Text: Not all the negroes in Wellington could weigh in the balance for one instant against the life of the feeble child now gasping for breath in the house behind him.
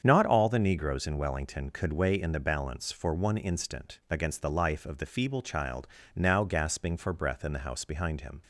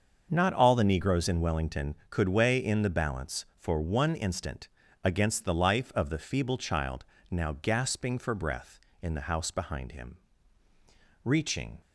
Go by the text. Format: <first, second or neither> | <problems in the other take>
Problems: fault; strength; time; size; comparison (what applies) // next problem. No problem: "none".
first | starts louder than the rest; until 1.3 s; 6.5 dB; strong in the first // pauses between "instant" and "against"; slight; at 4.6 s; 0.36 s long // pauses between "child" and "now"; slight; at 7.0 s; 0.28 s long; slight in the first // goes on to say "Reaching"; from 11.2 s on; 0.56 s long